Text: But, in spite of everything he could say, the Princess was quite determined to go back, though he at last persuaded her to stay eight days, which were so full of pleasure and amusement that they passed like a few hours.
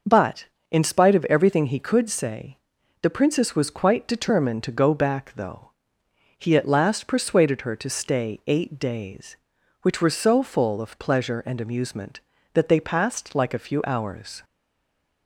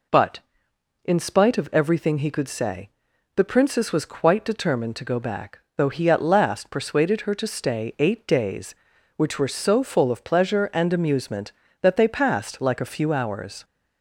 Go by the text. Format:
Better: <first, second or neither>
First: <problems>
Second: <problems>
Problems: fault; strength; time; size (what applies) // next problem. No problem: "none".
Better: second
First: pauses between "though" and "he"; noticeable; at 5.6 s; 0.66 s long // stays silent after the last word; slight; from 14.4 s on; 0.8 s long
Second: none